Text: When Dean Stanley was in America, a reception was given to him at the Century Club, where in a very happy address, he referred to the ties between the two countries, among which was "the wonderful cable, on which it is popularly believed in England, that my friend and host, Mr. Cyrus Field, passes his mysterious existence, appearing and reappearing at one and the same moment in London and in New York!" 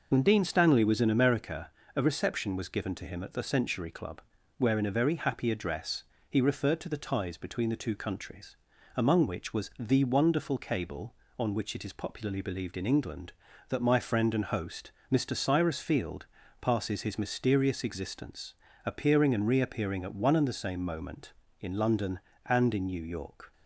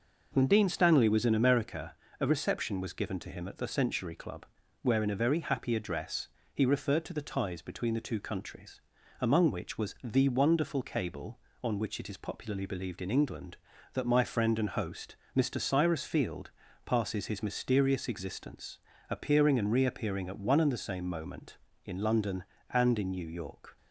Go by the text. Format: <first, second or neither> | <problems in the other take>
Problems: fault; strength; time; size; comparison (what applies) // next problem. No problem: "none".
second | loses the start of "When"; at 0.1 s; 35 ms